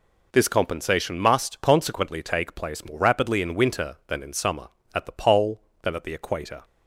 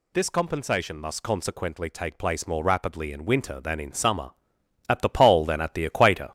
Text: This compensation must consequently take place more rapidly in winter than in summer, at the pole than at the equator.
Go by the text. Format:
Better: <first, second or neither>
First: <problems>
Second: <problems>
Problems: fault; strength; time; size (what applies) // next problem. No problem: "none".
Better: first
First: none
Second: gets louder; noticeable; throughout; 4.5 dB